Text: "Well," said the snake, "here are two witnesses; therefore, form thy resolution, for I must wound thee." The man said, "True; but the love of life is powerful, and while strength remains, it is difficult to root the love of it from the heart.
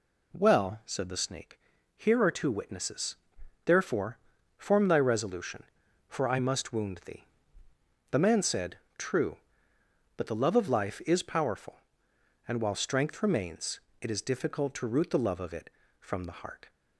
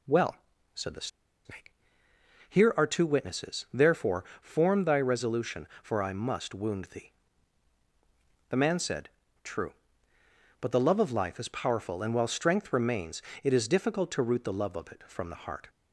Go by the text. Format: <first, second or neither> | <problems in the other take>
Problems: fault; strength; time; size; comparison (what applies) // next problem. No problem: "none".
first | pauses between "the" and "snake"; at 1.0 s; 0.38 s long